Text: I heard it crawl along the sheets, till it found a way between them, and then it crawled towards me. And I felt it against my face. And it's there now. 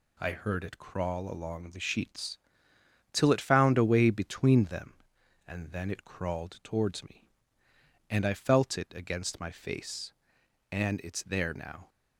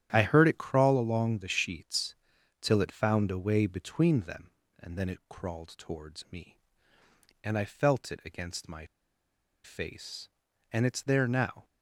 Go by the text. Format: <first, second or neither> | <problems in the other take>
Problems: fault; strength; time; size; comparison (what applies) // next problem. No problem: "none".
first | starts louder than the rest; strong; until 1.1 s; 10 dB // pauses between "my" and "face"; noticeable; at 8.8 s; 0.79 s long